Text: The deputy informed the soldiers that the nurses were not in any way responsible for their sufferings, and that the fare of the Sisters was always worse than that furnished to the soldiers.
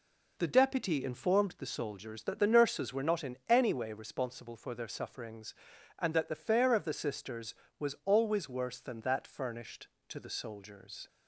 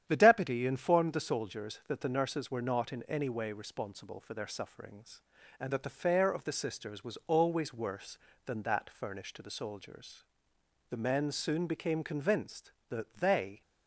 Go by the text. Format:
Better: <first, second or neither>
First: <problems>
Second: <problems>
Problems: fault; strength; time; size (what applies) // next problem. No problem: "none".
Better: first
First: none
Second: starts louder than the rest; strong; until 1.0 s; 9.5 dB // goes on to say "The men soon became convinced that they"; strong; from 10.8 s on; 2.7 s long